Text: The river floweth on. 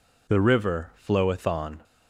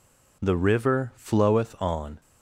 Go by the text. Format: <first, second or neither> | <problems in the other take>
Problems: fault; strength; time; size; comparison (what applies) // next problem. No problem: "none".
neither | none